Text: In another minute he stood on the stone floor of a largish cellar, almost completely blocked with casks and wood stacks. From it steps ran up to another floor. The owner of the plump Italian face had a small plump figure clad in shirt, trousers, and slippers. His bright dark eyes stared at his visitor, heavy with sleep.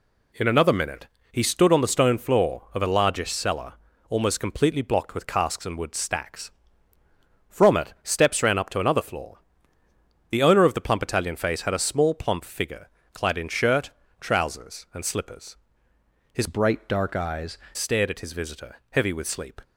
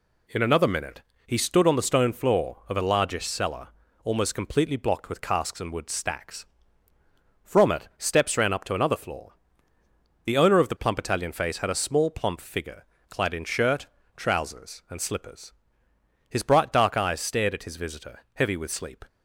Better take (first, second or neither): second